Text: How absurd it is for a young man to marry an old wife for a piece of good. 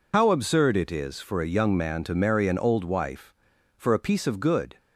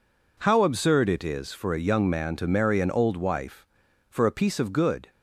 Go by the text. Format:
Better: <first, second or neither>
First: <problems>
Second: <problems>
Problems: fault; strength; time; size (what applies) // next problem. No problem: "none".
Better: second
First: loses the start of "How"; at 0.1 s; 70 ms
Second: none